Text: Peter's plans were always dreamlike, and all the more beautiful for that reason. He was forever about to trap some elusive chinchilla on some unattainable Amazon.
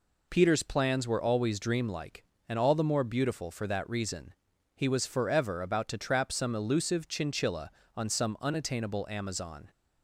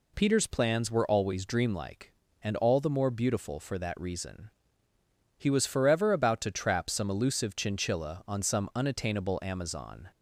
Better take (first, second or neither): neither